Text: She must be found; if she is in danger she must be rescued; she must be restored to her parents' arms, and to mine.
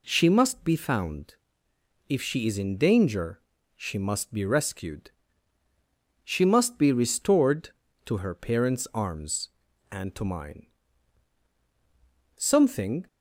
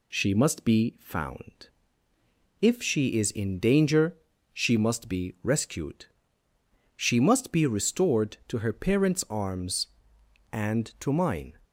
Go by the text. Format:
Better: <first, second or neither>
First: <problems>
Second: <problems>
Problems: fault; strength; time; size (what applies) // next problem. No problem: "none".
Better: second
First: pauses between "danger" and "she"; slight; at 3.3 s; 0.36 s long // goes on to say "Something"; noticeable; from 12.3 s on; 0.70 s long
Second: pauses between "danger" and "she"; slight; at 4.1 s; 0.34 s long